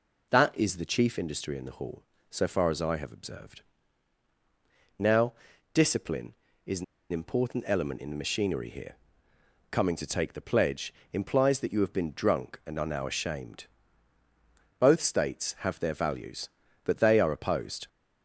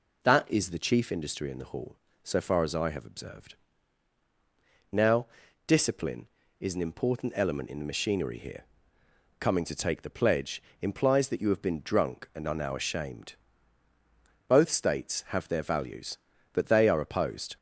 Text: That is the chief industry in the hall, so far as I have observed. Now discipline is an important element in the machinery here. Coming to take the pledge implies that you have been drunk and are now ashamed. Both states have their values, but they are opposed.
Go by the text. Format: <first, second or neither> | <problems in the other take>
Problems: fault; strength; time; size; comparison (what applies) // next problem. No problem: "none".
second | pauses between "Now" and "discipline"; at 5.3 s; 0.40 s long; also in the second // pauses between "an" and "important"; slight; at 6.8 s; 0.26 s long // pauses between "pledge" and "implies"; slight; at 10.9 s; 0.22 s long; slight in the second